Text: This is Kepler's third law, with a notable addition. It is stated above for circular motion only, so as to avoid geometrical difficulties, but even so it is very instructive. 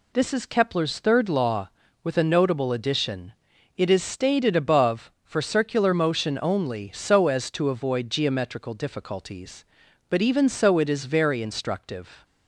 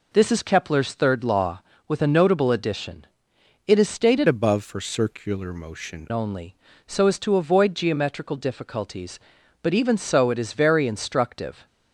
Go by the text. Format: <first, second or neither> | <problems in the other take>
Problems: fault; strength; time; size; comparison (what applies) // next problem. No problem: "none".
first | changes voice from "above" to "motion"; from 4.2 to 6.0 s; 1.8 s long